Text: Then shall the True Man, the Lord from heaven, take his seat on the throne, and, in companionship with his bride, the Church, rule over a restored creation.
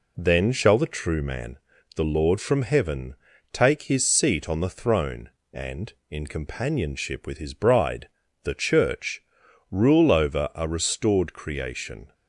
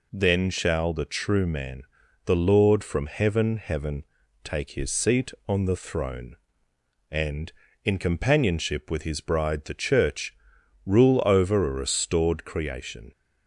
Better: first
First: none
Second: says "heaven" twice; at 3.5 s

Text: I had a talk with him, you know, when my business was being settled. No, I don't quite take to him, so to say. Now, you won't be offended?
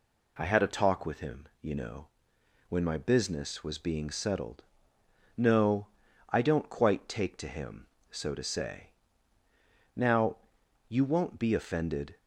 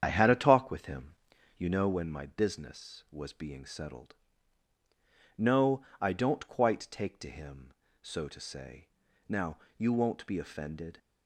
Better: first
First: none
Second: starts louder than the rest; strong; until 1.6 s; 8.5 dB

